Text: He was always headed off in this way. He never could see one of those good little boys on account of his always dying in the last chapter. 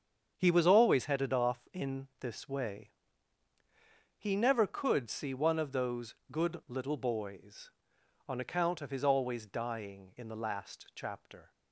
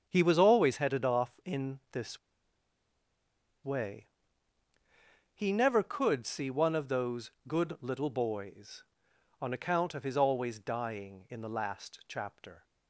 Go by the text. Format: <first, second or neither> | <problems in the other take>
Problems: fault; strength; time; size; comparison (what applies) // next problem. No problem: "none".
first | starts louder than the rest; strong; until 1.0 s; 7 dB; strong in the first // pauses between "this" and "way"; strong; at 2.1 s; 1.4 s long // pauses between "those" and "good"; slight; at 7.3 s; 0.16 s long; slight in the first